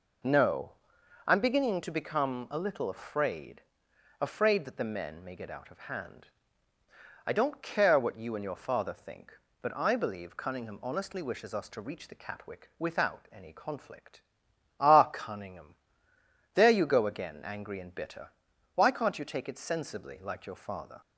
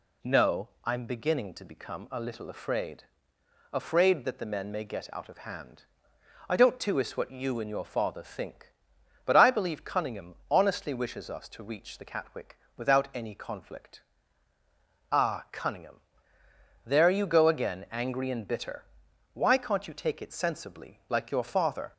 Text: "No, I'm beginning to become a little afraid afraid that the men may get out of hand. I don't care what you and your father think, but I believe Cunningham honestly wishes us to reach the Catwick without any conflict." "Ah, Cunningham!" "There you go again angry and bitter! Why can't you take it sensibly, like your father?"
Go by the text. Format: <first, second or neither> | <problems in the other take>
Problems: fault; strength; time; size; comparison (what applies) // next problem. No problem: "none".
first | pauses between "afraid" and "afraid"; noticeable; at 3.0 s; 0.68 s long; noticeable in the first // says "tuis" for "care"; at 6.7 s // pauses between "Cunningham" and "honestly"; slight; at 10.3 s; 0.16 s long // pauses between "Catwick" and "without"; slight; at 12.5 s; 0.20 s long